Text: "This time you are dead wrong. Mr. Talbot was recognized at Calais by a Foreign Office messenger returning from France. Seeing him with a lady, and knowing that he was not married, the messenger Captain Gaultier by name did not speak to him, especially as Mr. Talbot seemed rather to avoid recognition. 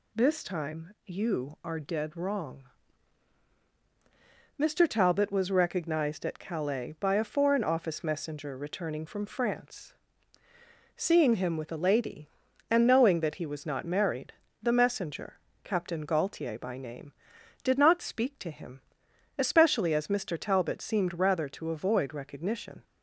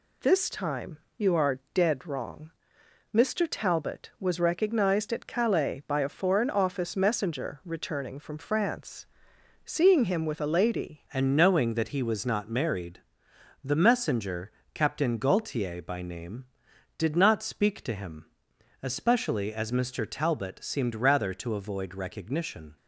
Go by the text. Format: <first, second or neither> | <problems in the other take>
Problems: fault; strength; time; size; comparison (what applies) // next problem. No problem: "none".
first | pauses between "time" and "you"; slight; at 0.9 s; 0.18 s long // changes voice at "and"; from 11.1 s on; 11.6 s long // pauses between "messenger" and "Captain"; slight; at 14.5 s; 0.22 s long; slight in the first